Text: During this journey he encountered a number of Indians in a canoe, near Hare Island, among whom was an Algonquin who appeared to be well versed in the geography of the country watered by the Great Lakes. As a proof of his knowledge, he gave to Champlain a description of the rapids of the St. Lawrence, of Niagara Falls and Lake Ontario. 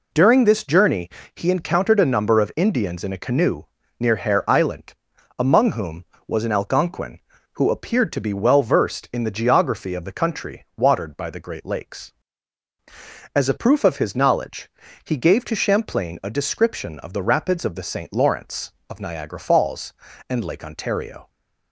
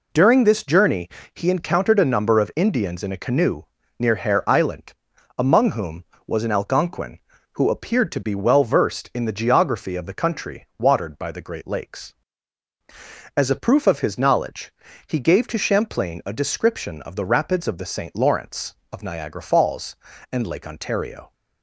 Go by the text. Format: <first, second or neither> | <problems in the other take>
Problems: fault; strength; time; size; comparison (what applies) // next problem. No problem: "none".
neither | pauses between "journey" and "he"; slight; the same in both